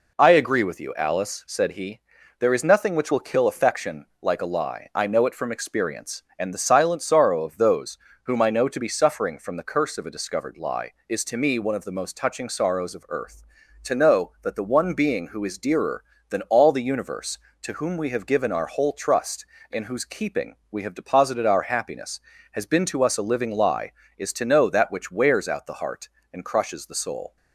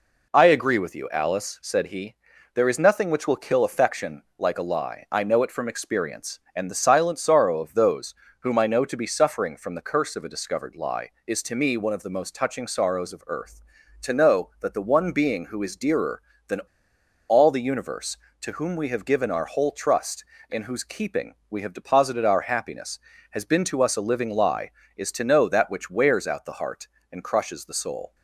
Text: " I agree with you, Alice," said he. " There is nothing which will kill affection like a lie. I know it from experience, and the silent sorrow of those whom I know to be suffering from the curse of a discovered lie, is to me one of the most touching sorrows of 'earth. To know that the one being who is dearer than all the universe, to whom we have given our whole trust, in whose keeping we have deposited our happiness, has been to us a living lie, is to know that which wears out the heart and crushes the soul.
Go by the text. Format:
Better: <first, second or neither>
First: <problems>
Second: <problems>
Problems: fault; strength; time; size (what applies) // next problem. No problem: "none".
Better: first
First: pauses between "those" and "whom"; slight; at 7.9 s; 0.26 s long // pauses between "keeping" and "we"; slight; at 20.5 s; 0.16 s long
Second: pauses between "those" and "whom"; slight; at 8.1 s; 0.26 s long // pauses between "than" and "all"; noticeable; at 16.6 s; 0.68 s long // pauses between "keeping" and "we"; slight; at 21.3 s; 0.16 s long